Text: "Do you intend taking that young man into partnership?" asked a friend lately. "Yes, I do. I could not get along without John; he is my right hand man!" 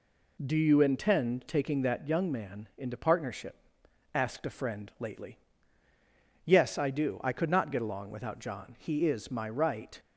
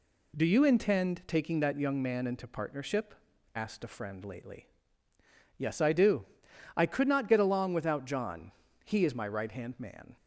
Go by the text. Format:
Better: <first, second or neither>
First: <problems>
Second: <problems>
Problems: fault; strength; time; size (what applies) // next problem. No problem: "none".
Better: second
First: stops before "hand man"; at 9.9 s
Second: none